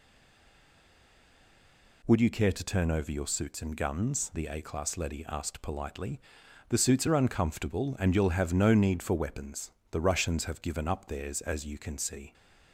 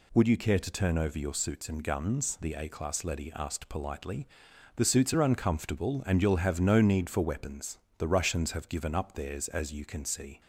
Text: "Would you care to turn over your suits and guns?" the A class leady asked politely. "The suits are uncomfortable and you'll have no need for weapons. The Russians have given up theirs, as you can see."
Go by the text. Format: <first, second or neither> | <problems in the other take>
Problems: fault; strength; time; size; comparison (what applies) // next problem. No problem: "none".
second | stays silent before the first word; noticeable; until 2.0 s; 2.0 s long